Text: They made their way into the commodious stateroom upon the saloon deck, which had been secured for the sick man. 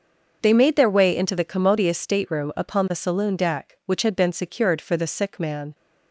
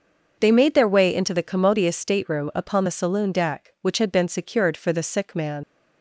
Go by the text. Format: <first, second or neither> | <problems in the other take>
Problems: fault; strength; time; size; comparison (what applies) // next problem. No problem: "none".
first | starts louder than the rest; until 1.4 s; 6 dB; also in the first // leaves "man" unfinished; at 5.6 s; 70 ms